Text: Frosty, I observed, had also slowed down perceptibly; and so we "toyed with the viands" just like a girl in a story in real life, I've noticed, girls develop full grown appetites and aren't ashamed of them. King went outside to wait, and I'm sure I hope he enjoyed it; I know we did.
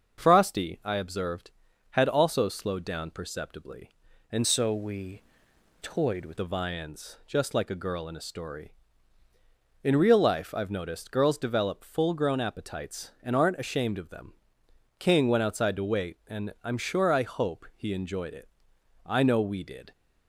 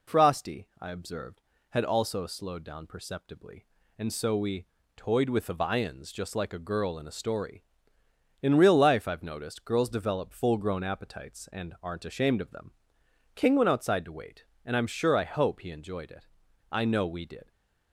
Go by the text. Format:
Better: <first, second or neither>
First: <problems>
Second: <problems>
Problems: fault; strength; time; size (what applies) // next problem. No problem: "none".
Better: second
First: starts louder than the rest; until 1.2 s; 6.5 dB // changes voice from "so" to "with"; from 4.4 to 6.3 s; 1.9 s long // pauses between "we" and "toyed"; noticeable; at 5.2 s; 0.62 s long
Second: pauses between "we" and "toyed"; slight; at 4.6 s; 0.32 s long